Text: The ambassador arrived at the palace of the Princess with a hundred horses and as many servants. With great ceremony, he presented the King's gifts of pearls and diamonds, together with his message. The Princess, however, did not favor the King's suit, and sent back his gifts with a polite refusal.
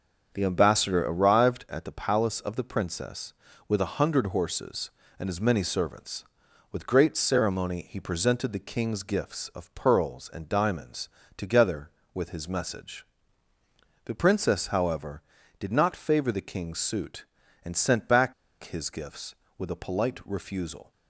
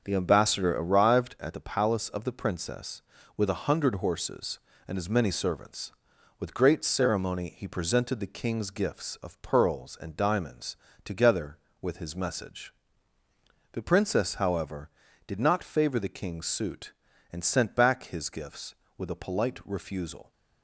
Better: second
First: starts louder than the rest; until 1.3 s; 6.5 dB // pauses between "back" and "his"; slight; at 18.3 s; 0.30 s long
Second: starts louder than the rest; until 1.0 s; 6.5 dB

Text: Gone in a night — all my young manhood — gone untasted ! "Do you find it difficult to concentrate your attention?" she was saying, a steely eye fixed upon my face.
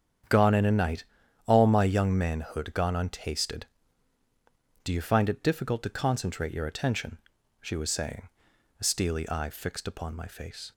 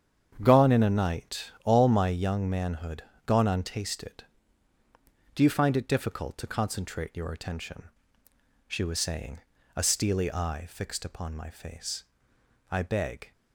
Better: first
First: starts louder than the rest; strong; until 1.7 s; 8.5 dB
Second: starts louder than the rest; strong; until 1.4 s; 8 dB // goes on to say "I beg"; from 12.7 s on; 0.60 s long

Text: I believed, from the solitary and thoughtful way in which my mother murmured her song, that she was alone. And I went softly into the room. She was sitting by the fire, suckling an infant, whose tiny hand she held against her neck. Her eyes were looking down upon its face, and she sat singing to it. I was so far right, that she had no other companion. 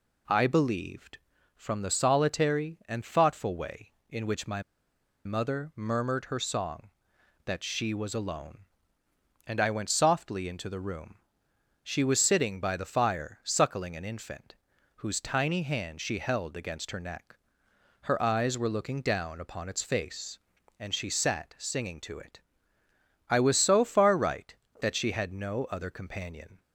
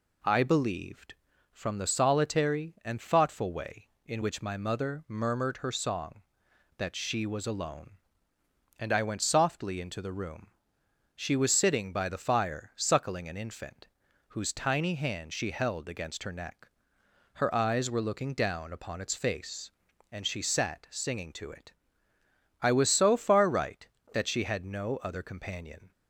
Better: second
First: pauses between "my" and "mother"; noticeable; at 4.6 s; 0.63 s long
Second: none

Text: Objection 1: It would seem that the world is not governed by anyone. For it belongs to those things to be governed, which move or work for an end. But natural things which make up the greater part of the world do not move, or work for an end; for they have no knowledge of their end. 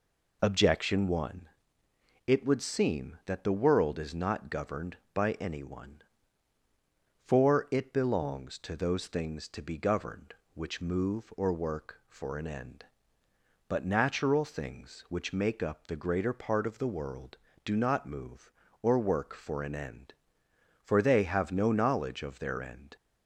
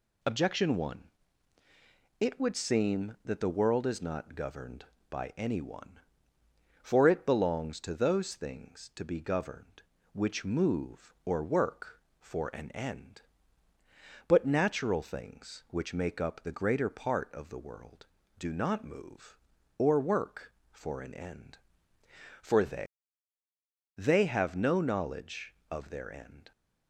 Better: first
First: none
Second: says "they" twice; at 23.9 s

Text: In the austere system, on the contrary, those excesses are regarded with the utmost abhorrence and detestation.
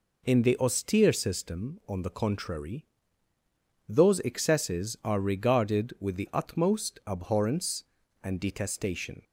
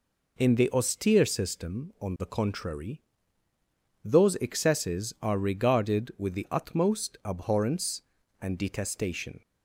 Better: neither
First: none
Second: none

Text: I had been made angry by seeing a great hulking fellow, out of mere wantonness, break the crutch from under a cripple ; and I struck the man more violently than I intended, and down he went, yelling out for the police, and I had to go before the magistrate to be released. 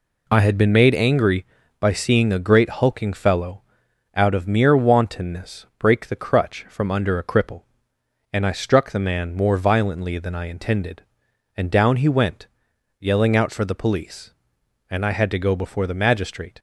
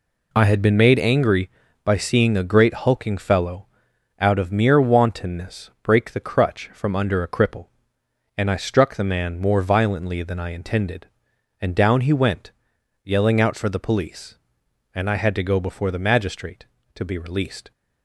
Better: second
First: stops before "to be released"; at 16.5 s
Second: none

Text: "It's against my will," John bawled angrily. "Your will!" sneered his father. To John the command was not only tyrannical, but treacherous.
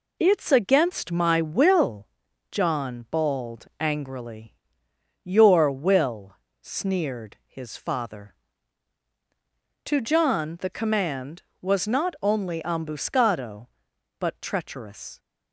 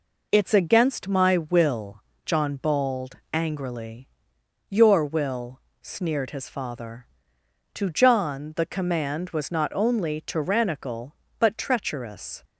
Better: second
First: says "ambuscado" for "tyrannical"; at 12.6 s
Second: none

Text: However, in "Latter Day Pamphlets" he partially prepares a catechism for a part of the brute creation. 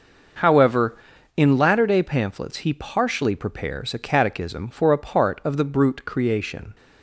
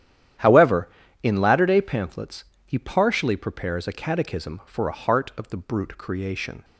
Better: first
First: starts louder than the rest; until 1.8 s; 6 dB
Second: starts louder than the rest; strong; until 1.7 s; 11 dB // pauses between "Pamphlets" and "he"; slight; at 2.4 s; 0.20 s long // says "heart" for "part"; at 4.9 s

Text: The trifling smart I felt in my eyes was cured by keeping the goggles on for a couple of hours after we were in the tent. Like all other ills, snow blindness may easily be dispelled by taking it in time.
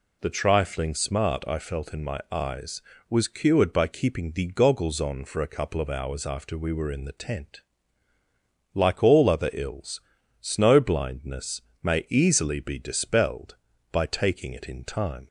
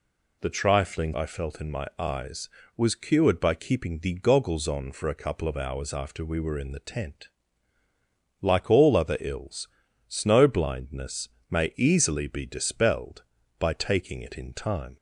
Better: first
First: pauses between "blindness" and "may"; slight; at 11.6 s; 0.22 s long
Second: skips "smart"; at 1.1 s // pauses between "blindness" and "may"; slight; at 11.2 s; 0.22 s long

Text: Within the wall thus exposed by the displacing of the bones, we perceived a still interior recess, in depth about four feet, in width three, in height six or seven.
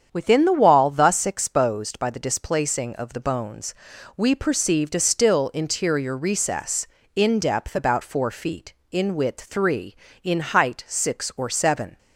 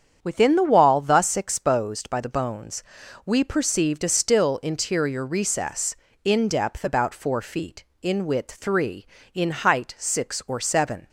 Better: first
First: starts louder than the rest; strong; until 1.1 s; 8 dB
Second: starts louder than the rest; strong; until 1.2 s; 8 dB // skips "the displacing of"; at 2.2 s

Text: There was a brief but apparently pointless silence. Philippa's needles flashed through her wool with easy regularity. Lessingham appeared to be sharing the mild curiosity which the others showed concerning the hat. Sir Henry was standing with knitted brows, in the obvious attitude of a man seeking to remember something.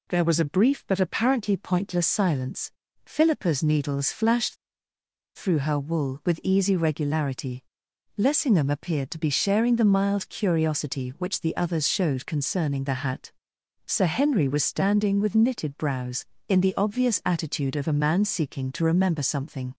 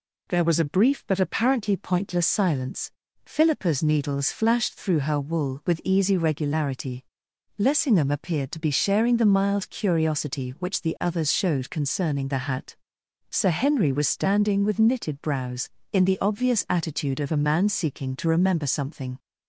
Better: second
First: pauses between "flashed" and "through"; noticeable; at 4.5 s; 0.79 s long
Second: none

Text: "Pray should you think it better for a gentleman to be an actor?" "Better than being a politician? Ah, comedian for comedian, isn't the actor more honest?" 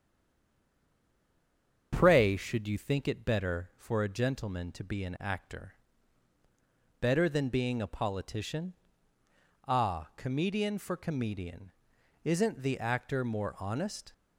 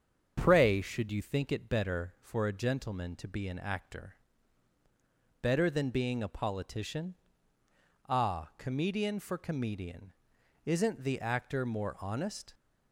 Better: second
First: stays silent before the first word; noticeable; until 1.9 s; 1.9 s long // starts louder than the rest; strong; until 2.9 s; 7.5 dB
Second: starts louder than the rest; strong; until 1.4 s; 7.5 dB

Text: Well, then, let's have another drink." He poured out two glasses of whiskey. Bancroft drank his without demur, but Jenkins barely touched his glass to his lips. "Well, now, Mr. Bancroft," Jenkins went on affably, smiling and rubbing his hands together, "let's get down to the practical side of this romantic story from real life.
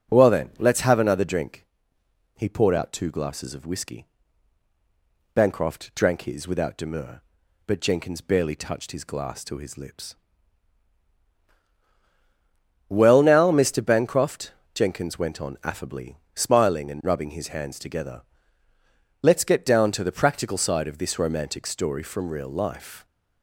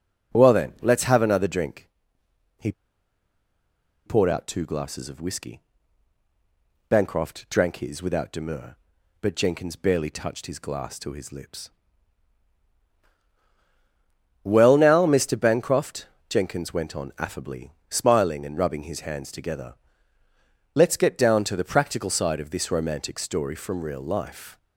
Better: first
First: none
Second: pauses between "He" and "poured"; strong; at 2.7 s; 1.3 s long

